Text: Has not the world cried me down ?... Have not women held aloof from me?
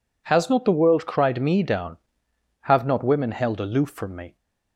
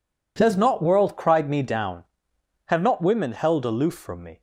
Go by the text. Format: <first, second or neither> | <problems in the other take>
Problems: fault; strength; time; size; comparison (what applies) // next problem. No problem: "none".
first | skips "the"; at 0.8 s